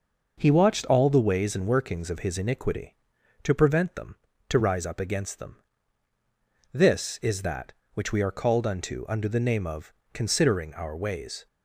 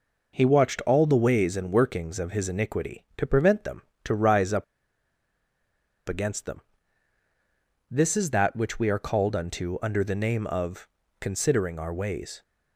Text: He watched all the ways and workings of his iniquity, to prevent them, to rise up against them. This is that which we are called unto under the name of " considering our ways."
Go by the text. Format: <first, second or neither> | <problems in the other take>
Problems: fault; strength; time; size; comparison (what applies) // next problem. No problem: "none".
first | pauses between "up" and "against"; strong; at 4.6 s; 1.4 s long